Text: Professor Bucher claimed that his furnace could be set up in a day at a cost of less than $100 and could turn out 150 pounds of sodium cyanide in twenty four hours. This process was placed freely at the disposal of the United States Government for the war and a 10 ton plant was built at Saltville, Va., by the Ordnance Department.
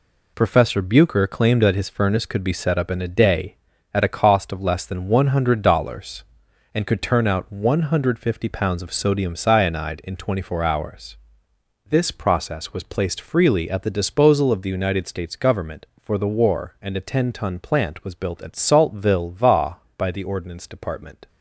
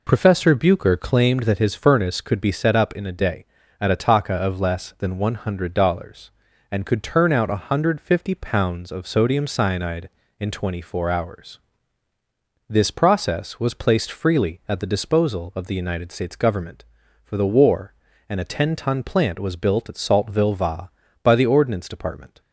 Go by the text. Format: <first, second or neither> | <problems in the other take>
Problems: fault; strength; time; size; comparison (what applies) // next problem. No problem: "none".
first | says "taka" for "cost"; at 3.9 s